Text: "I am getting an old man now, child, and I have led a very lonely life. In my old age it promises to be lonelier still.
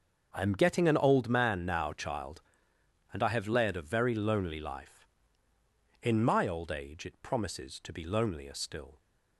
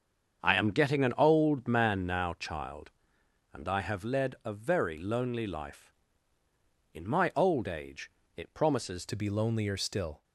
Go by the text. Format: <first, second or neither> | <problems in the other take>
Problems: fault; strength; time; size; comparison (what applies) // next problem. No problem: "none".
first | starts louder than the rest; strong; until 1.4 s; 7 dB; also in the first // pauses between "age" and "it"; slight; at 8.1 s; 0.24 s long // changes voice at "to"; from 9.0 s on; 1.2 s long